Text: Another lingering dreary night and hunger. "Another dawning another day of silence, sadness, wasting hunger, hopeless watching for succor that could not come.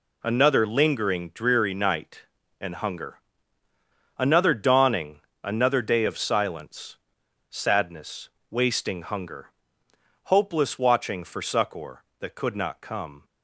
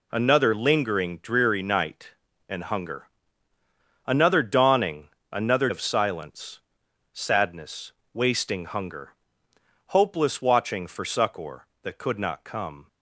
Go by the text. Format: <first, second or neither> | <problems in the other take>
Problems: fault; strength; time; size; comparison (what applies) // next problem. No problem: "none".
first | pauses between "dawning" and "another"; slight; at 5.0 s; 0.22 s long; slight in the first // skips "day"; at 5.6 s